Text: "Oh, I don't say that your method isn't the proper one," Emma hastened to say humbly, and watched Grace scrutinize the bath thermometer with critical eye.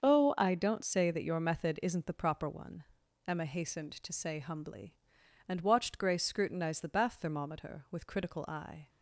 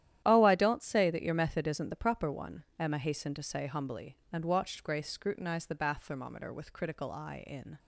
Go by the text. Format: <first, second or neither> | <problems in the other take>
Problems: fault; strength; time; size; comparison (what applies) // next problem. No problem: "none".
first | starts louder than the rest; strong; until 1.2 s; 11.5 dB; also in the first // goes on to say "In"; slight; from 7.4 s on; 0.32 s long